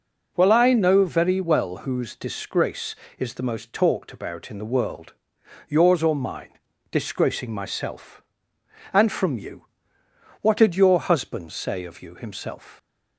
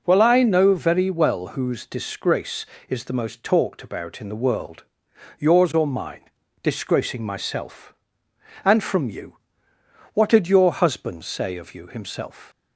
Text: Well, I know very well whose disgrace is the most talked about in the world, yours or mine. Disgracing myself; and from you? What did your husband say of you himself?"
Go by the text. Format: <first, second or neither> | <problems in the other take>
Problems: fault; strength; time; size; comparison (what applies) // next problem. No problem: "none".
neither | none